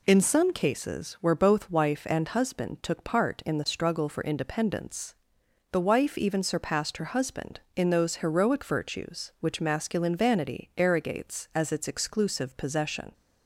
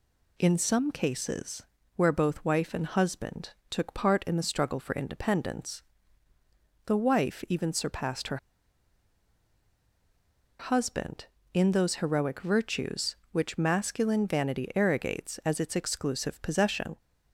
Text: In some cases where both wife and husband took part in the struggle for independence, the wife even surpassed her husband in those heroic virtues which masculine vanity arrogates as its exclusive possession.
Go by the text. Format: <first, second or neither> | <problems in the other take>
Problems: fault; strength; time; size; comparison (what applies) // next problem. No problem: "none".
first | pauses between "cases" and "where"; slight; at 1.6 s; 0.34 s long // pauses between "husband" and "took"; slight; at 3.5 s; 0.20 s long // pauses between "her" and "husband"; strong; at 8.3 s; 2.2 s long